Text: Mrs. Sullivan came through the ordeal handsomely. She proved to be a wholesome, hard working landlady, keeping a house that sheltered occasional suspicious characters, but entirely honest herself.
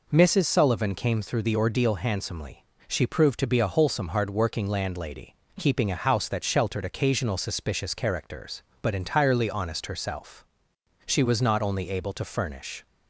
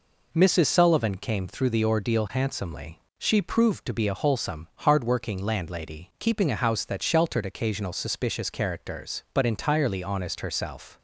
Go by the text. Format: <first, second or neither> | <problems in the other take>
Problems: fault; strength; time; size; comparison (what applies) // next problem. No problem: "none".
second | goes on to say "She was not only able to furnish"; strong; from 11.0 s on; 1.8 s long